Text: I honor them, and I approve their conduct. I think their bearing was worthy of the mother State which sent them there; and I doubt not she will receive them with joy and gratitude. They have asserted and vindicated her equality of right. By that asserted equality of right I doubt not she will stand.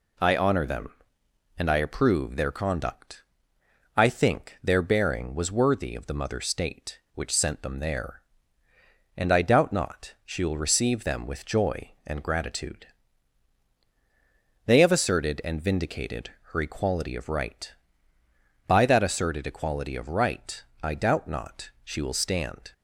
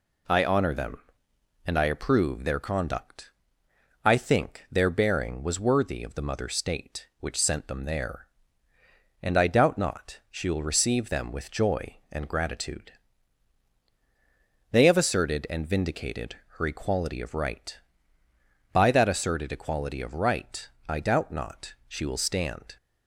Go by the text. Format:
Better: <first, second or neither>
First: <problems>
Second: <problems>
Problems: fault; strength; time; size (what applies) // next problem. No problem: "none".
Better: neither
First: pauses between "vindicated" and "her"; slight; at 16.3 s; 0.20 s long // pauses between "right" and "I"; slight; at 20.6 s; 0.20 s long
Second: pauses between "vindicated" and "her"; slight; at 16.3 s; 0.20 s long // pauses between "right" and "I"; slight; at 20.6 s; 0.20 s long